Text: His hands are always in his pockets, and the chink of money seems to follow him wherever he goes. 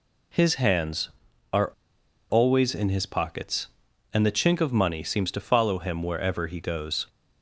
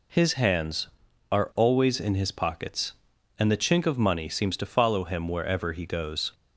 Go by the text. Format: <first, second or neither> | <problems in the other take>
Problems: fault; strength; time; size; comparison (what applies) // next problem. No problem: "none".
second | pauses between "are" and "always"; noticeable; at 1.7 s; 0.60 s long